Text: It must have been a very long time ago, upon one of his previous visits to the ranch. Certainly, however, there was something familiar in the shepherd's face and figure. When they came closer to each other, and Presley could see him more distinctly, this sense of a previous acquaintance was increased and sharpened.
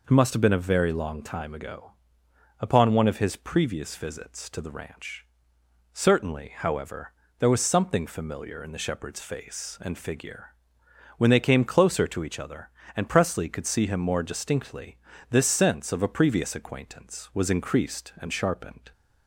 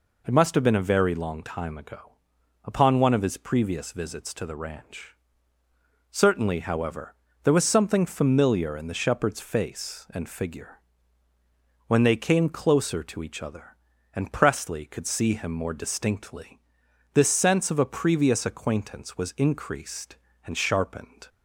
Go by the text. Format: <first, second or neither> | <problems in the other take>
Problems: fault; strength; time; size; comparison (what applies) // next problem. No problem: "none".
neither | none